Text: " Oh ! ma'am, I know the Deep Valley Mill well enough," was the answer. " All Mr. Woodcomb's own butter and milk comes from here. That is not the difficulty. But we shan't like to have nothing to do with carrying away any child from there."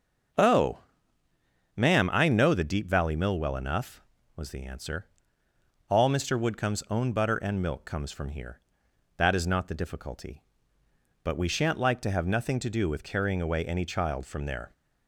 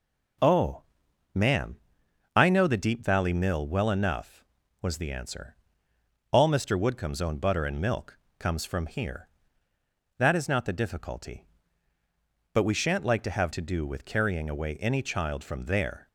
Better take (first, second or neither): first